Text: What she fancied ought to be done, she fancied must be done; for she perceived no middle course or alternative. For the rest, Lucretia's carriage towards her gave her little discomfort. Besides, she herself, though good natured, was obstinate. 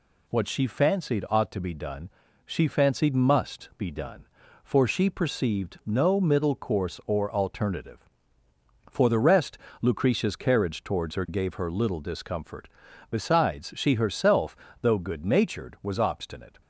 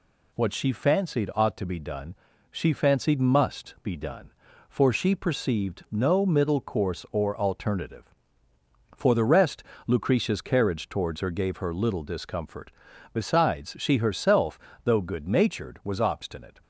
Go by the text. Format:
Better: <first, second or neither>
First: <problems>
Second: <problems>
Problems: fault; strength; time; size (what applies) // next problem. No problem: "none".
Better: neither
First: none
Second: none